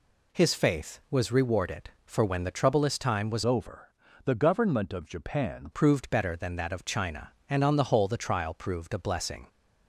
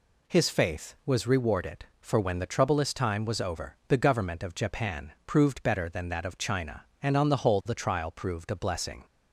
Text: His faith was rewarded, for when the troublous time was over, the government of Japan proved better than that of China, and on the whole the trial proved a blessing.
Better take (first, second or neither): second